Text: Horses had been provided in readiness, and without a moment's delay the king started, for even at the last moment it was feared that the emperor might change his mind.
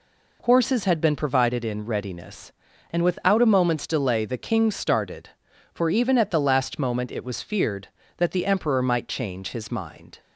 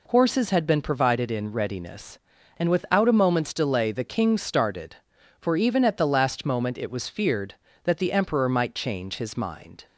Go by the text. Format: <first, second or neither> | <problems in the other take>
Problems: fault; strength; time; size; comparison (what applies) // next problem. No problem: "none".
neither | none